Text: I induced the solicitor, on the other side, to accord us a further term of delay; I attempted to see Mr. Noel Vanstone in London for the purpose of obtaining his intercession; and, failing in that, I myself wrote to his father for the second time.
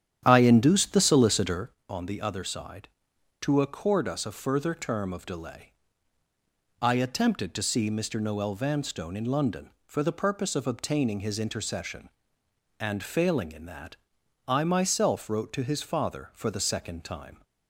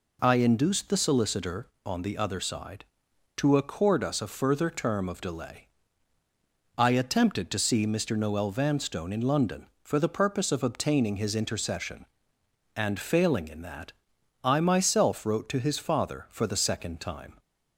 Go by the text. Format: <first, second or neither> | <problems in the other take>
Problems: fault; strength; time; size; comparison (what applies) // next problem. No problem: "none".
second | starts louder than the rest; strong; until 1.7 s; 10 dB